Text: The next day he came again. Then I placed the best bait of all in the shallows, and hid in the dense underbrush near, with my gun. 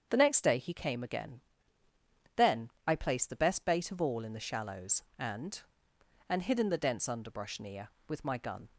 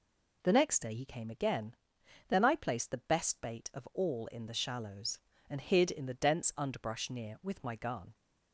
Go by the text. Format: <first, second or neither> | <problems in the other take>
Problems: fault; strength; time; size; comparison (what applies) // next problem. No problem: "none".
second | starts louder than the rest; strong; until 1.1 s; 7.5 dB // pauses between "Then" and "I"; slight; at 2.6 s; 0.16 s long // says "and" twice; at 6.2 s